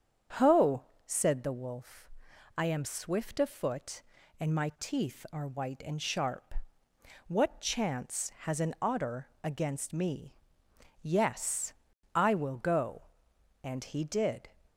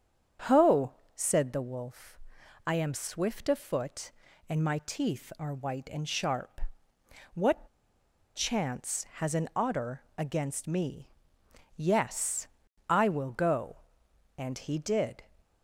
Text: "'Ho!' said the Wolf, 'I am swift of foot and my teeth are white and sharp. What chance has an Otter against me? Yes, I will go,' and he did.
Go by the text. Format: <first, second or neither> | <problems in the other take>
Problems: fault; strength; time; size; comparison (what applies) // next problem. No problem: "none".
first | starts louder than the rest; strong; until 1.6 s; 7 dB; strong in the first // pauses between "What" and "chance"; noticeable; at 7.6 s; 0.69 s long // pauses between "Otter" and "against"; slight; at 10.0 s; 0.16 s long; slight in the first